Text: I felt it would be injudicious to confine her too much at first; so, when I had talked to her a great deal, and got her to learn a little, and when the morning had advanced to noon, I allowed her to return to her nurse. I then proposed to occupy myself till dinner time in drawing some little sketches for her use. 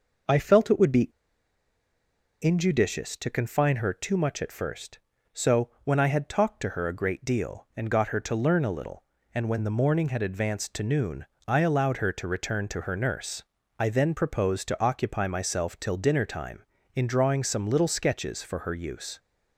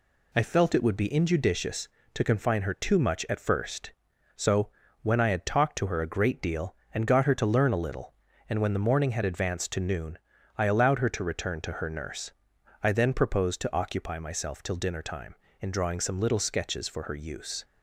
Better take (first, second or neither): second